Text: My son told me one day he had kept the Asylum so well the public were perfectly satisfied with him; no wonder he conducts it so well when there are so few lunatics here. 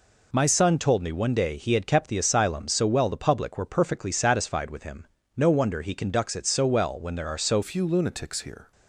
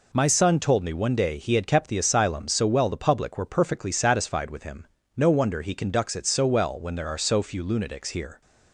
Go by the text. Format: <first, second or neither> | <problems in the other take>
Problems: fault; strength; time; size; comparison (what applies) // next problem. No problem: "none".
second | changes voice at "few"; from 7.6 s on; 1.1 s long